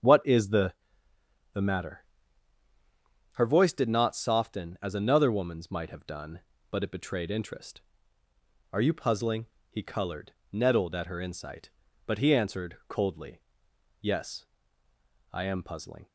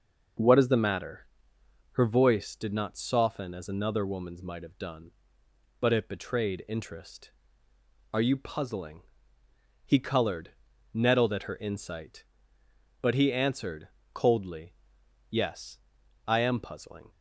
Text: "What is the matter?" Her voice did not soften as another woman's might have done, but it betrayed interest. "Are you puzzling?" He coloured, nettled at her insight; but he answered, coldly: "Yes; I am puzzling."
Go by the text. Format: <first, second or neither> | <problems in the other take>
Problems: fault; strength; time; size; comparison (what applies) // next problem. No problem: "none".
second | starts louder than the rest; strong; until 1.8 s; 7.5 dB // says "the" twice; at 1.5 s